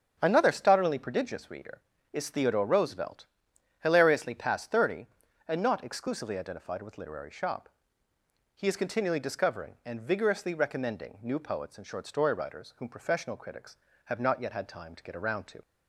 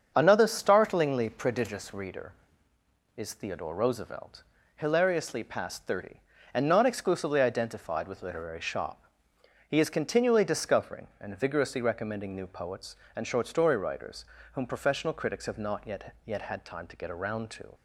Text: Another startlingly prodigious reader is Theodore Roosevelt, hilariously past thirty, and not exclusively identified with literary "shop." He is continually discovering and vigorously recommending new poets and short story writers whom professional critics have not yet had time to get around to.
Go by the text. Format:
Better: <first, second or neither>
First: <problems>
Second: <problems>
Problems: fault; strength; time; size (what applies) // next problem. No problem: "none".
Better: first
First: starts louder than the rest; strong; until 1.2 s; 7.5 dB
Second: starts louder than the rest; strong; until 1.1 s; 7.5 dB // pauses between "writers" and "whom"; slight; at 14.2 s; 0.28 s long // says "yet" twice; at 16.2 s